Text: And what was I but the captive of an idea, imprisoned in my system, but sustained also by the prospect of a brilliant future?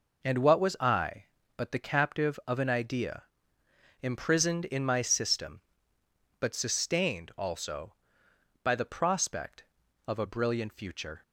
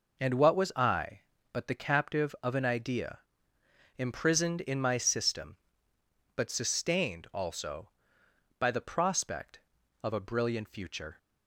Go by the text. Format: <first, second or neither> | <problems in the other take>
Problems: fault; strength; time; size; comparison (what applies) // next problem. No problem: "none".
neither | none